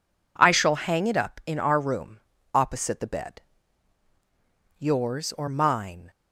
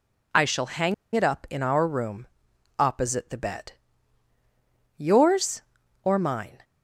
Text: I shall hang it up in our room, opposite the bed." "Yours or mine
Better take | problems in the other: first | pauses between "hang" and "it"; slight; at 0.9 s; 0.21 s long

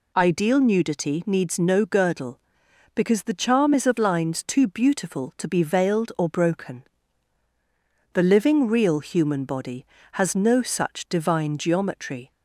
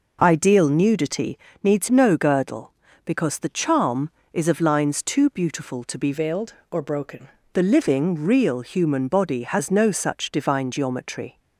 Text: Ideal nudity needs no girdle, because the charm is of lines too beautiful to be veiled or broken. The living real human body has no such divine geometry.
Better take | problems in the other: first | pauses between "nudity" and "needs"; slight; at 1.3 s; 0.26 s long // changes voice from "veiled" to "broken"; from 6.1 to 7.2 s; 1.1 s long

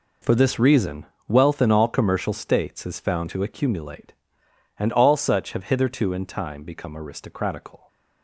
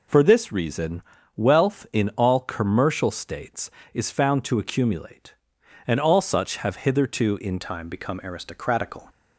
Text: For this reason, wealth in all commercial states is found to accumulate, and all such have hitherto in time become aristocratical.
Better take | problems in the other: first | changes voice at "time"; from 7.6 s on; 1.4 s long

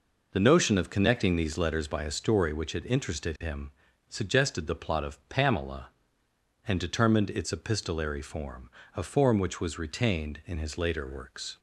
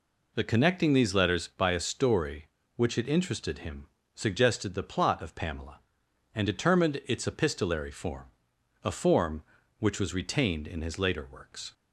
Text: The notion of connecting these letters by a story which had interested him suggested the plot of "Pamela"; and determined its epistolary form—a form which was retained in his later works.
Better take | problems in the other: first | skips "notion of"; at 0.4 s // pauses between "him" and "suggested"; slight; at 3.8 s; 0.28 s long; also in the first

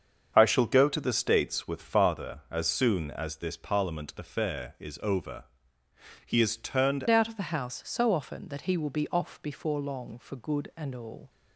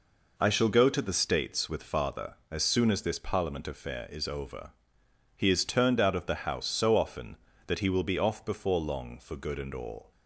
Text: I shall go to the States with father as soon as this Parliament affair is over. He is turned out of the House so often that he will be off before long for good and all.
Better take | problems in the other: second | starts louder than the rest; until 1.3 s; 7 dB // changes voice at "out"; from 7.0 s on; 4.2 s long

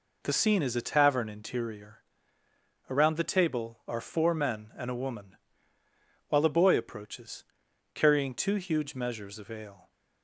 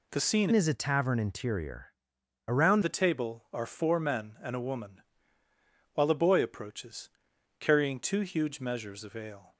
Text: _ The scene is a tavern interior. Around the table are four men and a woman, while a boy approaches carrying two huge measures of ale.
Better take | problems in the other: first | changes voice from "is" to "Around"; from 0.5 to 2.8 s; 2.3 s long // pauses between "approaches" and "carrying"; noticeable; at 7.0 s; 0.50 s long; noticeable in the first

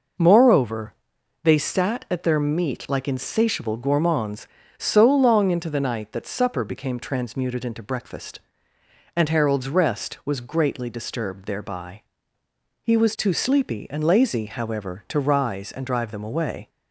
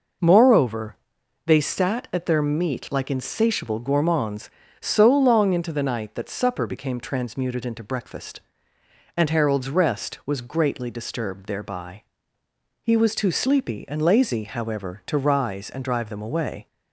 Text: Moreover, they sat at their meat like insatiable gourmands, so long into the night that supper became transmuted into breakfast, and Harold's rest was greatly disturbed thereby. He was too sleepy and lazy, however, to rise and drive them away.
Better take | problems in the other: neither | none

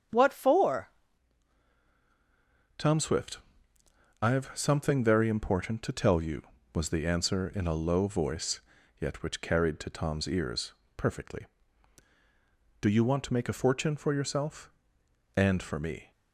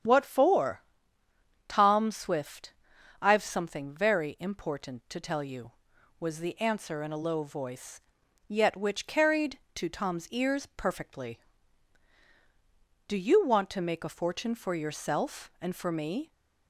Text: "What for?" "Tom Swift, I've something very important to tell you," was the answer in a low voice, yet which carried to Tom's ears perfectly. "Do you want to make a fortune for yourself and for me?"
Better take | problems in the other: second | starts louder than the rest; strong; until 2.9 s; 7.5 dB; strong in the second // changes voice at "Tom"; from 2.7 s on; 13.4 s long // pauses between "ears" and "perfectly"; slight; at 10.7 s; 0.24 s long

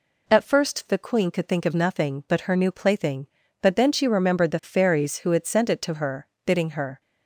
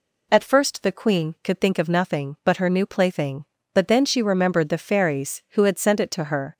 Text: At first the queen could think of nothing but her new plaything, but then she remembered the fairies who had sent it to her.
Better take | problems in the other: second | goes on to say "Bidding her"; from 6.4 s on; 0.54 s long

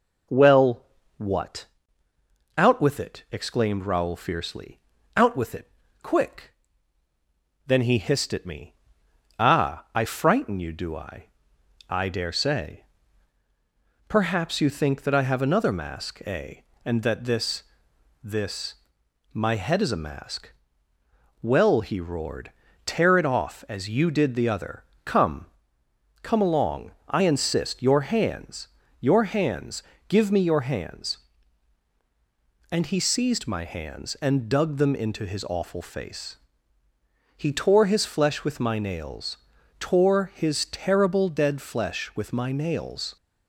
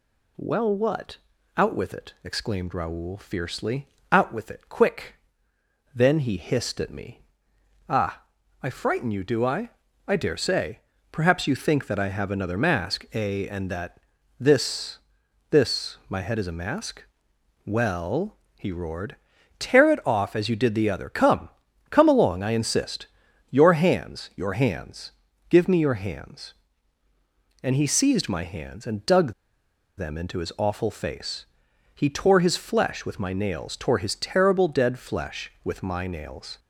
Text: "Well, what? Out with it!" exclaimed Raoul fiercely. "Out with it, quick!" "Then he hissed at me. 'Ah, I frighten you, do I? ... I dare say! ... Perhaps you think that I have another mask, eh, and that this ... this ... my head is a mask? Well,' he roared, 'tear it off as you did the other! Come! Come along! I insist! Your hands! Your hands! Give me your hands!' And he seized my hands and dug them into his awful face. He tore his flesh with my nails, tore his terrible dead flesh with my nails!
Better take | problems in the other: first | pauses between "that" and "this"; at 14.0 s; 0.38 s long // pauses between "dug" and "them"; noticeable; at 29.3 s; 0.64 s long

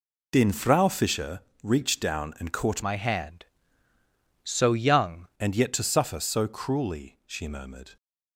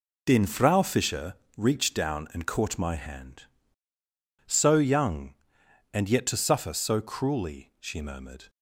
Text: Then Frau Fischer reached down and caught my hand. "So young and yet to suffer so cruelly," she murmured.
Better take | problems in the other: second | pauses between "Fischer" and "reached"; slight; at 1.4 s; 0.22 s long; slight in the second // changes voice from "my" to "young"; from 2.8 to 5.2 s; 2.4 s long

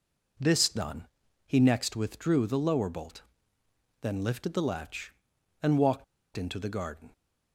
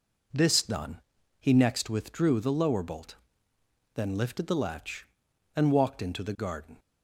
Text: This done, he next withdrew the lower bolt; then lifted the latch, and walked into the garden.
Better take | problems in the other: second | pauses between "walked" and "into"; slight; at 6.0 s; 0.32 s long

